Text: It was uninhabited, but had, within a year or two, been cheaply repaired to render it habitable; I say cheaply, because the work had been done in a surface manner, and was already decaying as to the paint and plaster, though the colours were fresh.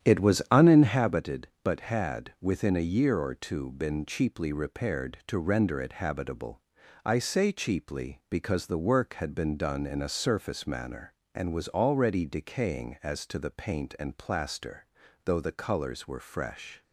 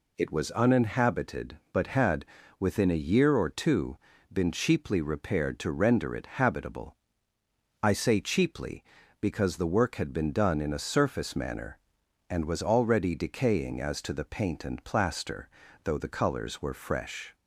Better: second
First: starts louder than the rest; strong; until 1.2 s; 10 dB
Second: none

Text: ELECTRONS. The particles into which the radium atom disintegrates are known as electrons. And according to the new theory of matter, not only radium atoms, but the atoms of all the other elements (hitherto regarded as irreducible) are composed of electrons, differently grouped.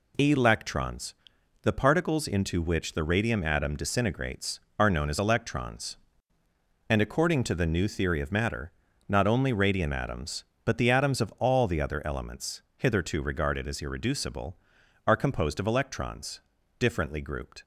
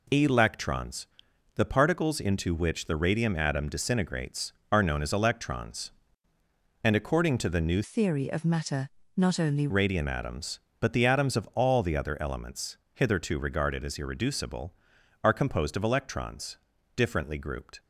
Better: first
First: none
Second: changes voice from "theory" to "only"; from 7.8 to 9.6 s; 1.8 s long

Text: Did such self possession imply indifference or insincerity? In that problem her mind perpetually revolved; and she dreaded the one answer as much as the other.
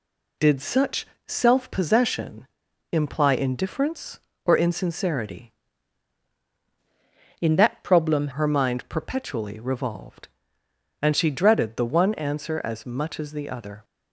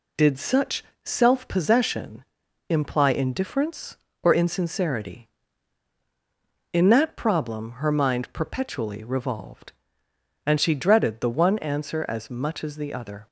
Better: second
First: pauses between "such" and "self"; slight; at 1.0 s; 0.20 s long // pauses between "possession" and "imply"; noticeable; at 2.4 s; 0.46 s long // changes voice from "In" to "problem"; from 7.3 to 8.2 s; 0.9 s long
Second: pauses between "such" and "self"; slight; at 0.8 s; 0.20 s long // pauses between "possession" and "imply"; noticeable; at 2.2 s; 0.46 s long

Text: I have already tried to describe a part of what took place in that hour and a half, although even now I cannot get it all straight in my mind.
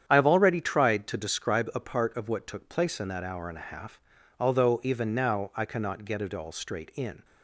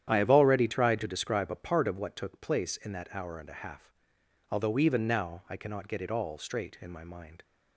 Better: second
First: starts louder than the rest; strong; until 1.0 s; 9 dB // stops before "my mind"; at 7.2 s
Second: starts louder than the rest; strong; until 1.1 s; 10 dB

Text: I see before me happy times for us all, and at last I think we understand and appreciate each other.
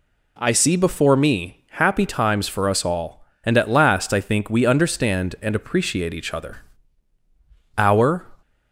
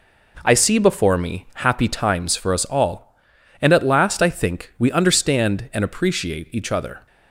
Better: second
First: goes on to say "Our"; slight; from 7.7 s on; 0.48 s long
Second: none

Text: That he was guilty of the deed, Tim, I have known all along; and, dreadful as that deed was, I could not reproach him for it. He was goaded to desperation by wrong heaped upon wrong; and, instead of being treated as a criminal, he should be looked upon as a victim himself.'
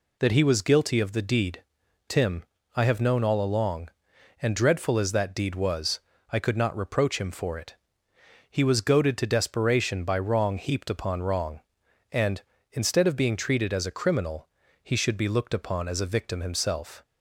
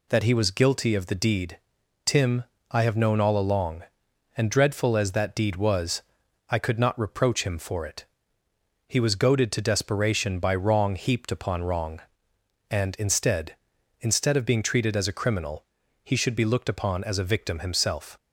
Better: first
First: none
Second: says "instead" twice; at 13.9 s

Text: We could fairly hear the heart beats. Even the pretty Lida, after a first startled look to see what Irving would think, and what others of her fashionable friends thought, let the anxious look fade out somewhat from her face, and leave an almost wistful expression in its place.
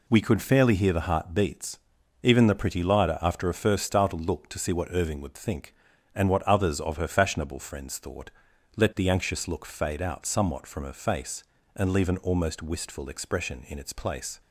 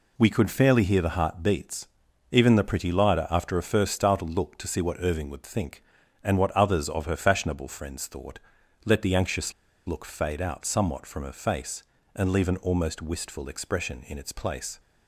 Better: first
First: none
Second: pauses between "anxious" and "look"; slight; at 9.5 s; 0.34 s long

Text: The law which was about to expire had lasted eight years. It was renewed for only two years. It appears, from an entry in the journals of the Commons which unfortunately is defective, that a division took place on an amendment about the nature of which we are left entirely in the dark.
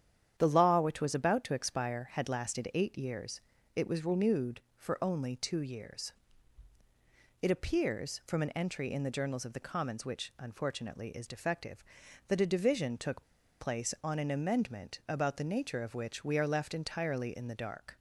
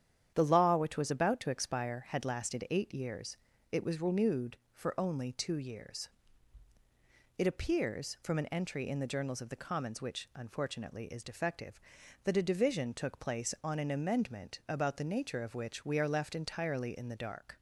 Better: second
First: starts louder than the rest; strong; until 1.3 s; 9.5 dB // pauses between "took" and "place"; at 13.2 s; 0.37 s long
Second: starts louder than the rest; strong; until 1.3 s; 9.5 dB

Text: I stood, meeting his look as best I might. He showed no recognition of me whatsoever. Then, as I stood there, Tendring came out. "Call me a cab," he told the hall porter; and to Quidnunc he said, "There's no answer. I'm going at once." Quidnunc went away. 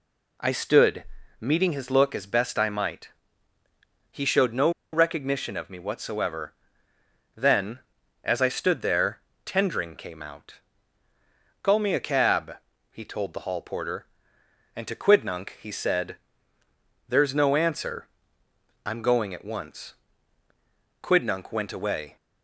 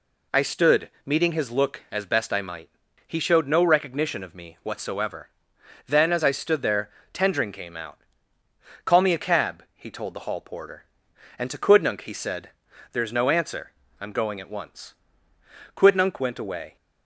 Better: second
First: pauses between "no" and "recognition"; slight; at 4.6 s; 0.23 s long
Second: none

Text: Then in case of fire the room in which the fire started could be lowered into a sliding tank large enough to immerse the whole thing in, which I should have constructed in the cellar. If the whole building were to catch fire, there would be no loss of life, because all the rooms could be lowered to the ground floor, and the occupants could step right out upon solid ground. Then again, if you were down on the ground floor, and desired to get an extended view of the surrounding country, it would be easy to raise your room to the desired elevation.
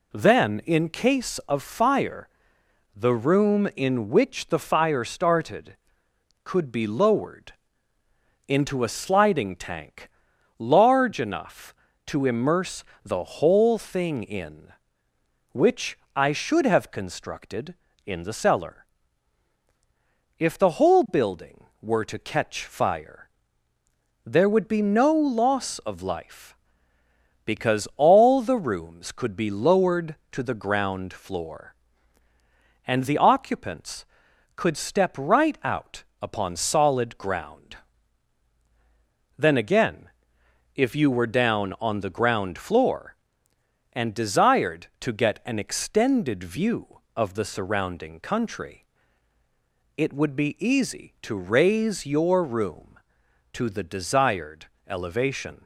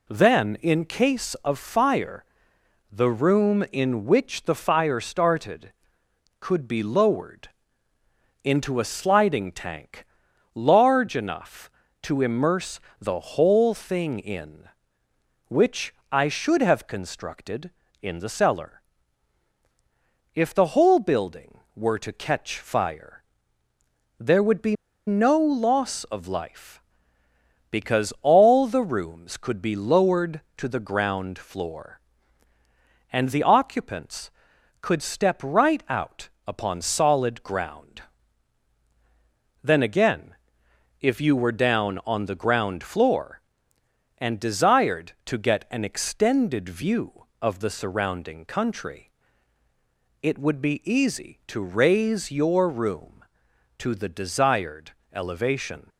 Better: first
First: pauses between "fire" and "the"; noticeable; at 2.2 s; 0.66 s long // pauses between "lowered" and "into"; noticeable; at 7.5 s; 0.94 s long // pauses between "tank" and "large"; noticeable; at 10.0 s; 0.50 s long // pauses between "immerse" and "the"; slight; at 12.8 s; 0.22 s long // pauses between "which" and "I"; slight; at 15.9 s; 0.18 s long // pauses between "out" and "upon"; slight; at 36.0 s; 0.18 s long // pauses between "desired" and "elevation"; slight; at 54.6 s; 0.22 s long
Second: pauses between "fire" and "the"; noticeable; at 2.2 s; 0.66 s long // pauses between "lowered" and "into"; noticeable; at 7.4 s; 0.94 s long // pauses between "tank" and "large"; noticeable; at 10.0 s; 0.50 s long // pauses between "immerse" and "the"; slight; at 12.7 s; 0.22 s long // pauses between "which" and "I"; slight; at 15.9 s; 0.18 s long // pauses between "be" and "no"; slight; at 24.7 s; 0.33 s long // pauses between "out" and "upon"; slight; at 36.2 s; 0.18 s long // pauses between "desired" and "elevation"; slight; at 54.9 s; 0.22 s long

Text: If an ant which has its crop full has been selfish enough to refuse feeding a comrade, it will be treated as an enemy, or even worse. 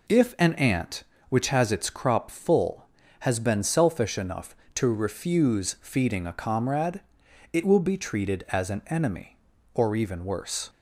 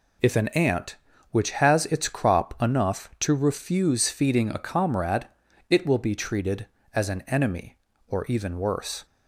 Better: first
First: none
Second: skips "full has been selfish"; at 2.5 s

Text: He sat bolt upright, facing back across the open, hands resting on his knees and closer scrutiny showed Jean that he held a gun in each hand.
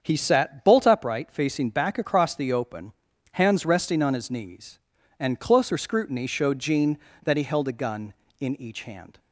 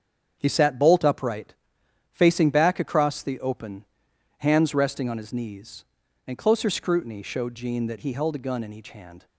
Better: neither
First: starts louder than the rest; until 1.0 s; 7 dB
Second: starts louder than the rest; strong; until 1.4 s; 7.5 dB

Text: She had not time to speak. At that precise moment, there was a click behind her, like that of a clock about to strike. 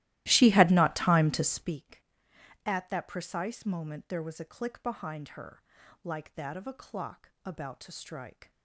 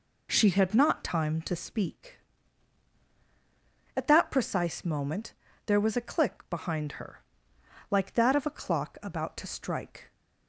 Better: second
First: starts louder than the rest; strong; until 1.7 s; 16 dB // pauses between "clock" and "about"; slight; at 7.2 s; 0.16 s long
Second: none

